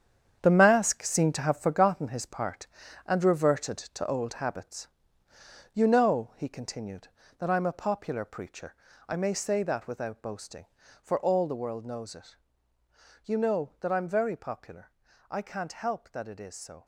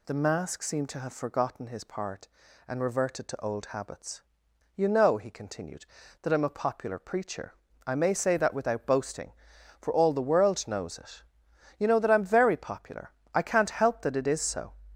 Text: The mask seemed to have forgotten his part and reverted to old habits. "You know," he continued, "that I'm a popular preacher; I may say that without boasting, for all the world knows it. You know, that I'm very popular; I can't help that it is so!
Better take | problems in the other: second | gets quieter; strong; throughout; 10 dB

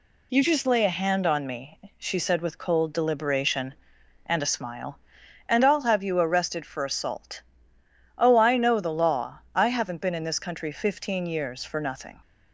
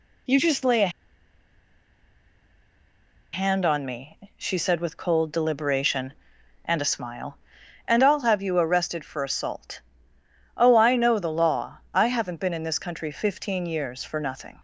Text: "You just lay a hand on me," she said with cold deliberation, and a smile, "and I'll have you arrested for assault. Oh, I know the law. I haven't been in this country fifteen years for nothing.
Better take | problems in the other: first | pauses between "a" and "hand"; strong; at 0.8 s; 2.4 s long

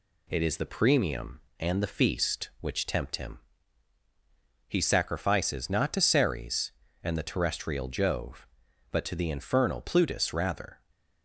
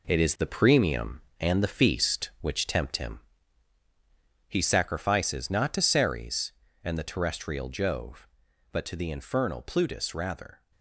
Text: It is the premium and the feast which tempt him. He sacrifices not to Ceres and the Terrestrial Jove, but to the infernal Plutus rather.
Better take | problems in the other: first | gets quieter; throughout; 7 dB

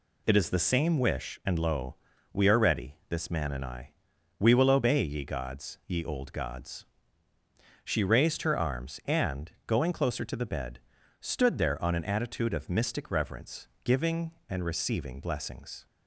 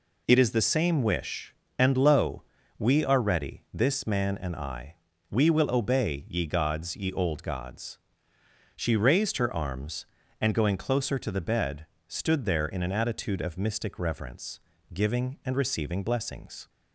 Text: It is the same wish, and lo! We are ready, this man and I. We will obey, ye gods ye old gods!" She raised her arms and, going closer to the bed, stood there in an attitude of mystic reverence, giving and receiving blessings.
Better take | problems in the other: second | says "on" for "in"; at 11.8 s

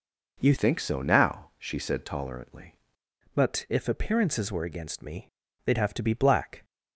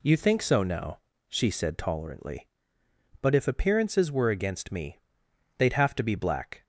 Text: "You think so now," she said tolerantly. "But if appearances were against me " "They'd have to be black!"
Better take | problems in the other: second | changes voice from "think" to "tolerantly"; from 0.5 to 2.7 s; 2.2 s long

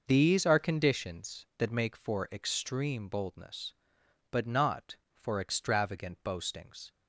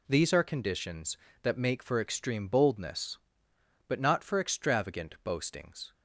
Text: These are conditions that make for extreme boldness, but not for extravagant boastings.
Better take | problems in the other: neither | none

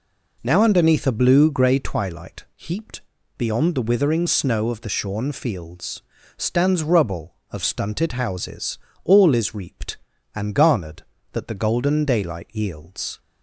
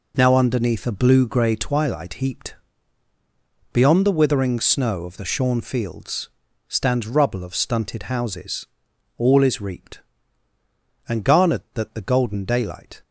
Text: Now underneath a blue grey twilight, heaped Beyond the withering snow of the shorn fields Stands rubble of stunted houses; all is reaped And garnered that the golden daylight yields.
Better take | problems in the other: first | pauses between "heaped" and "Beyond"; at 2.5 s; 1.1 s long; slight in the first // pauses between "fields" and "Stands"; at 6.2 s; 0.38 s long; slight in the first // stops before "yields"; at 13.0 s

